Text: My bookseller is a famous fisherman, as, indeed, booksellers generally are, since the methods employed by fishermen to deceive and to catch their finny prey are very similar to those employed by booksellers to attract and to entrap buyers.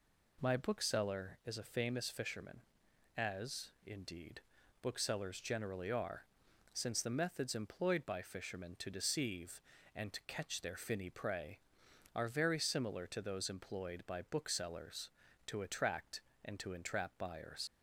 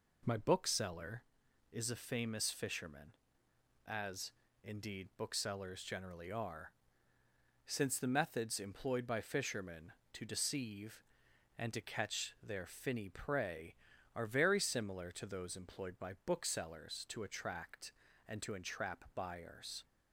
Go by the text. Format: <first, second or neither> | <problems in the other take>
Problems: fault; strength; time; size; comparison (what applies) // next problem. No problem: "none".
second | leaves "buyers" unfinished; at 17.6 s; 60 ms